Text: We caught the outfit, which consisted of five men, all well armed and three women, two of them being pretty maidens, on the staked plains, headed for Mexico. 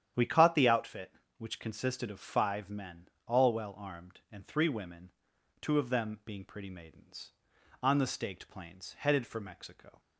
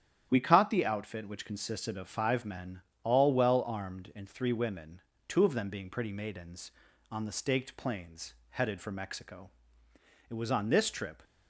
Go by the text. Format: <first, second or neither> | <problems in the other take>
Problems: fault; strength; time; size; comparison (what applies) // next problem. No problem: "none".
first | starts louder than the rest; strong; until 1.3 s; 10 dB; strong in the first // goes on to say "It was on this trip"; noticeable; from 10.2 s on; 0.94 s long